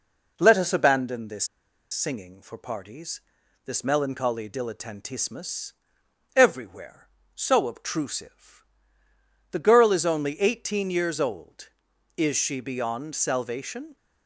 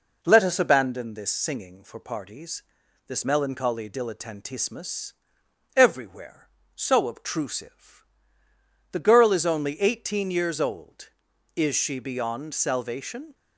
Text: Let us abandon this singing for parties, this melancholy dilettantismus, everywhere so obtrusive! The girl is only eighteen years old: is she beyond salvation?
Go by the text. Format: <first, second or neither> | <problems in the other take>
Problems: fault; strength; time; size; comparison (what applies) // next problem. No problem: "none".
second | pauses between "this" and "singing"; noticeable; at 1.4 s; 0.45 s long